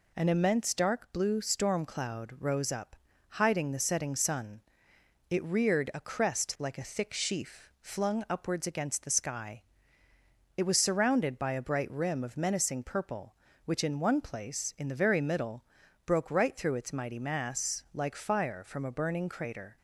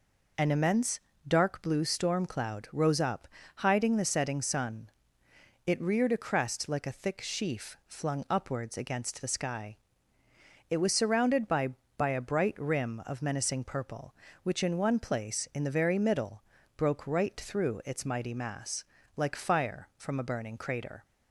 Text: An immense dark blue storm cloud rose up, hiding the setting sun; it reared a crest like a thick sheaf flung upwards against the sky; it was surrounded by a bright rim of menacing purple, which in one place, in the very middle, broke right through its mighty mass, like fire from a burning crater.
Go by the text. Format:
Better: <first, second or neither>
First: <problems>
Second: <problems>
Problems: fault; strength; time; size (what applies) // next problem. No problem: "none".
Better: first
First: none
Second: pauses between "immense" and "dark"; slight; at 0.9 s; 0.26 s long // says "by" twice; at 11.9 s